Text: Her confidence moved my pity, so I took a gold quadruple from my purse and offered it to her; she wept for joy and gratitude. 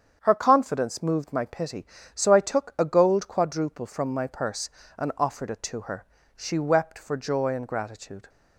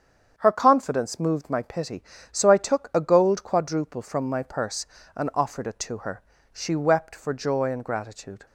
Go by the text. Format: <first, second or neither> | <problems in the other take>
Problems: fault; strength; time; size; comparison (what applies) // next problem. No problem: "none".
neither | starts louder than the rest; strong; the same in both